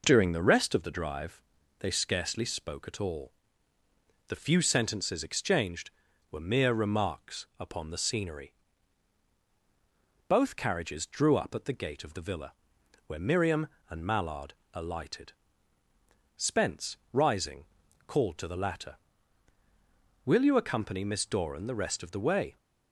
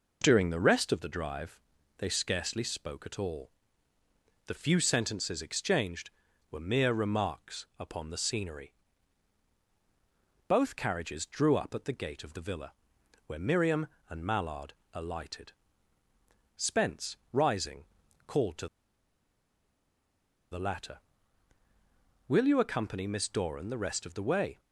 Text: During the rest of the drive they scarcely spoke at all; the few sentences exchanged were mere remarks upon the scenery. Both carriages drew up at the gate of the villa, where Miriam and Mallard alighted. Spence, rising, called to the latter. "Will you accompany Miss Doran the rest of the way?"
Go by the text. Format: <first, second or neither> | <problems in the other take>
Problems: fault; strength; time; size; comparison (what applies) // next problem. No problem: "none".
first | pauses between "drive" and "they"; at 1.5 s; 0.40 s long; also in the first // pauses between "Mallard" and "alighted"; slight; at 14.7 s; 0.18 s long; slight in the first // pauses between "to" and "the"; strong; at 18.6 s; 1.8 s long